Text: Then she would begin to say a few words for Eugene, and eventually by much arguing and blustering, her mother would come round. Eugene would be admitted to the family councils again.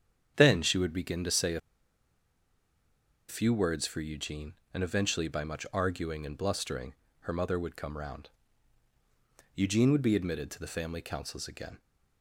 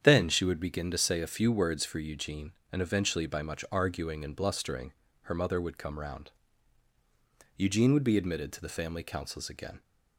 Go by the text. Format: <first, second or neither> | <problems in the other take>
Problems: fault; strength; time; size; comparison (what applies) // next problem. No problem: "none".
second | starts louder than the rest; strong; until 1.3 s; 8.5 dB; strong in the second // pauses between "a" and "few"; strong; at 1.6 s; 1.6 s long